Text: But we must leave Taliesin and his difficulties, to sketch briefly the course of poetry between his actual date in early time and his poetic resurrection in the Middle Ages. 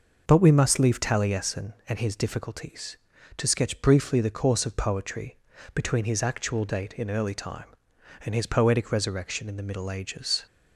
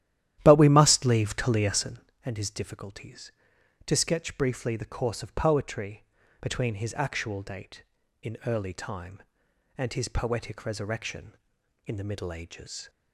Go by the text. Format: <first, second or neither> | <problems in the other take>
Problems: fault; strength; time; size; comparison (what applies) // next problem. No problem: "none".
first | starts louder than the rest; strong; until 2.2 s; 12 dB // pauses between "poetry" and "between"; at 6.0 s; 0.38 s long; also in the first